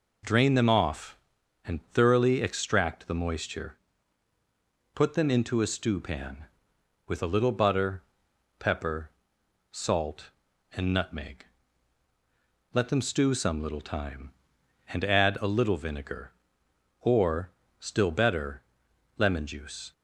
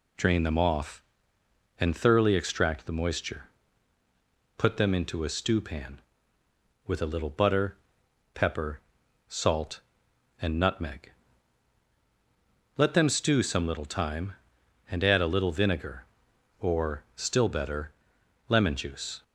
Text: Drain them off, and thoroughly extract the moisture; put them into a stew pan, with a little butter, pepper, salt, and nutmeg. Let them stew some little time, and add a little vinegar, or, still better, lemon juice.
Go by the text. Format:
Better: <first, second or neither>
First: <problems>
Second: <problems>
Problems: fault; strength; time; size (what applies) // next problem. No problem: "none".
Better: neither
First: none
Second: none